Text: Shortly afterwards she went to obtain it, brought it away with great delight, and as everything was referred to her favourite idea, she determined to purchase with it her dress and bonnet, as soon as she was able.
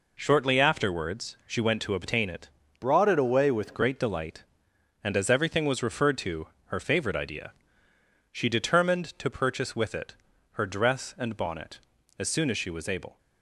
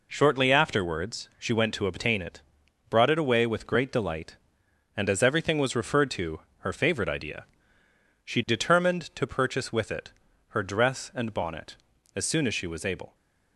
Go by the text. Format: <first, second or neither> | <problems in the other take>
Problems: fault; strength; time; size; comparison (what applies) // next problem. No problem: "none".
second | changes voice from "brought" to "with"; from 2.8 to 3.7 s; 0.9 s long // pauses between "to" and "her"; slight; at 6.4 s; 0.18 s long; slight in the second // pauses between "it" and "her"; at 10.1 s; 0.38 s long; also in the second